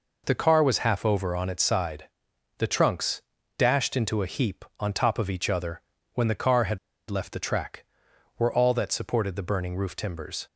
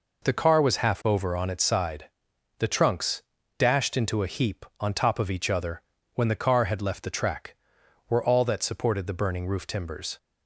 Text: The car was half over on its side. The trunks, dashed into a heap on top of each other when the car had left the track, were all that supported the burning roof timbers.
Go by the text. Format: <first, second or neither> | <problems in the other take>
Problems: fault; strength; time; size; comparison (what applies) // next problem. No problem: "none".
second | pauses between "other" and "when"; slight; at 5.8 s; 0.30 s long; slight in the second // pauses between "had" and "left"; slight; at 6.7 s; 0.32 s long